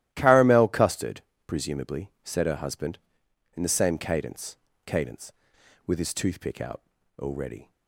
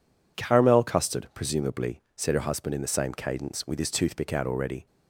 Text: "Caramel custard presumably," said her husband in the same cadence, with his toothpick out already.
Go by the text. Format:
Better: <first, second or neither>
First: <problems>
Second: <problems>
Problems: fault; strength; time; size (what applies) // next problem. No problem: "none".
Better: second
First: starts louder than the rest; strong; until 1.1 s; 13.5 dB // pauses between "custard" and "presumably"; slight; at 1.2 s; 0.24 s long // says "cadence" twice; at 4.8 s // pauses between "out" and "already"; slight; at 6.8 s; 0.36 s long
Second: none